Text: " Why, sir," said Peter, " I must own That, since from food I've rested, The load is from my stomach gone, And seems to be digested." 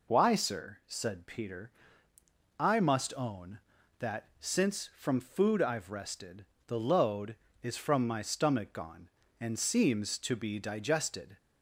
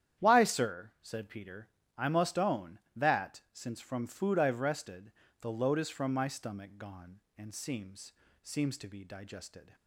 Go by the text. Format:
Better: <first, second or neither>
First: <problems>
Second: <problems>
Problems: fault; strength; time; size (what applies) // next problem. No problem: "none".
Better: first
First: none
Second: starts louder than the rest; strong; until 1.2 s; 10 dB // says "seems" twice; at 8.4 s